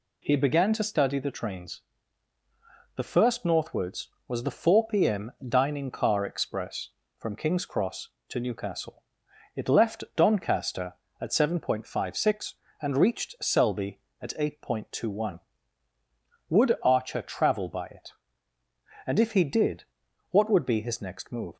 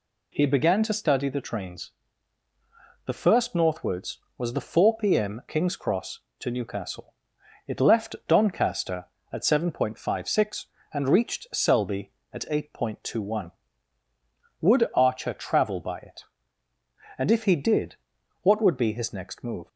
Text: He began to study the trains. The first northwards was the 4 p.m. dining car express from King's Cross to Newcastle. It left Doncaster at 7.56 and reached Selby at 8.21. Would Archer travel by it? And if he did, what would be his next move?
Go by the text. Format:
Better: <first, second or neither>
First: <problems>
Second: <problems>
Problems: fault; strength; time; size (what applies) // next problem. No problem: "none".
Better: first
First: none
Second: skips "dining car express from"; at 5.4 s